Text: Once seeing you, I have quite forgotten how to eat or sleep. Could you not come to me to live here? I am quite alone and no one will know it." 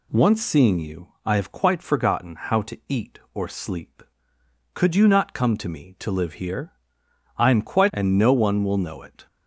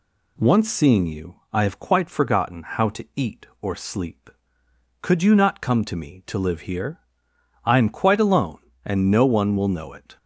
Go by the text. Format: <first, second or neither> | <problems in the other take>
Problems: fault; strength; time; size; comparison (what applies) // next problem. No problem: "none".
second | skips "alone"; at 7.9 s